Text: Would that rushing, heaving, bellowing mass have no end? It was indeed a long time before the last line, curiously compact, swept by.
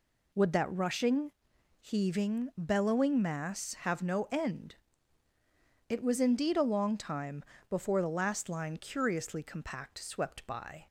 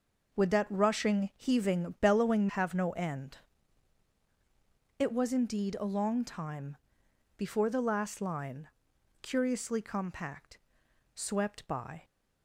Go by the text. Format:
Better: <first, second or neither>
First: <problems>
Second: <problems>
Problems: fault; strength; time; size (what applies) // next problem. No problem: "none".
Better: first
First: pauses between "time" and "before"; slight; at 7.4 s; 0.24 s long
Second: skips "mass"; at 2.4 s // pauses between "time" and "before"; noticeable; at 6.7 s; 0.60 s long